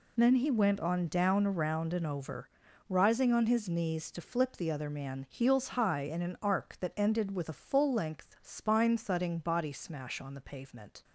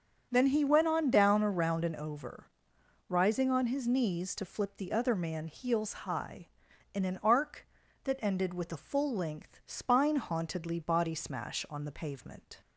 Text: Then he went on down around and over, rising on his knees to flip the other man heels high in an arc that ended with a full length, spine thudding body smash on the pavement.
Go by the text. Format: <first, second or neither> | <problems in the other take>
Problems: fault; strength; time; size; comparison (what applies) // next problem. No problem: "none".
first | starts louder than the rest; strong; until 1.3 s; 7.5 dB // says "hauntedly" for "thudding"; at 10.1 s